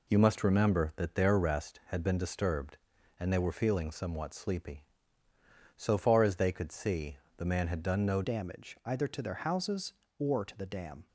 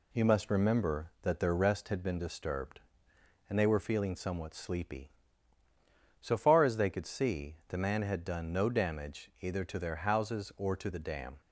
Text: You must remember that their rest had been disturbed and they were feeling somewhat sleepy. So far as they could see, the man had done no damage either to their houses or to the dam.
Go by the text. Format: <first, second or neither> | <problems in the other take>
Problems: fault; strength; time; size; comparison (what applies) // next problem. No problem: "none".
second | changes voice at "damage"; from 8.2 s on; 2.8 s long